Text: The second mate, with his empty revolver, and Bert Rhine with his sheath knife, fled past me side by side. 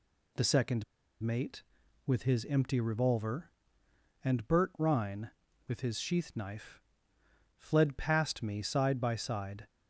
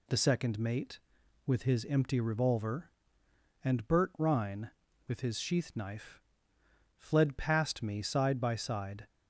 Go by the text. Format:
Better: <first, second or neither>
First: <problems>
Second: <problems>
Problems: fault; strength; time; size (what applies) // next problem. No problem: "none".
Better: second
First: pauses between "second" and "mate"; at 0.8 s; 0.39 s long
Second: none